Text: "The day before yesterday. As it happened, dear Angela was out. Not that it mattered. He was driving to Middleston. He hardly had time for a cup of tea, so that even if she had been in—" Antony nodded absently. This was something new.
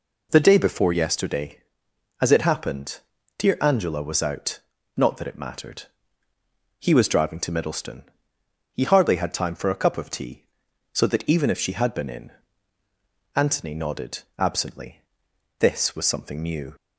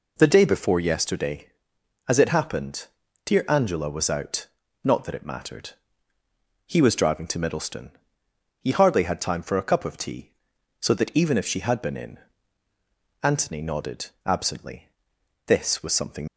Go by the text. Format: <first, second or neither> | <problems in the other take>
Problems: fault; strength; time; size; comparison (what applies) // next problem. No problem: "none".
first | stops before "new"; at 16.2 s